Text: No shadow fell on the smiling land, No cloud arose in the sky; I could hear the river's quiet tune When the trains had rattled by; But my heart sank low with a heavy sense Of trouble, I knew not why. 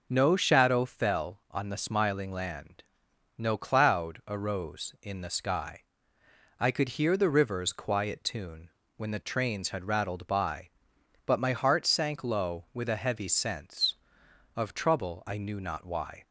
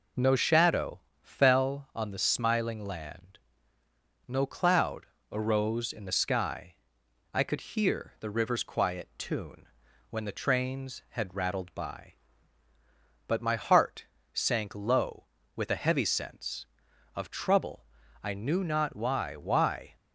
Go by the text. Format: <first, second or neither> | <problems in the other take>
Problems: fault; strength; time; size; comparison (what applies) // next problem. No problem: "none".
first | pauses between "shadow" and "fell"; slight; at 1.0 s; 0.20 s long // pauses between "cloud" and "arose"; slight; at 5.0 s; 0.22 s long // pauses between "tune" and "When"; at 9.6 s; 0.44 s long; slight in the first // pauses between "heart" and "sank"; slight; at 14.0 s; 0.30 s long // says "why" twice; at 19.3 s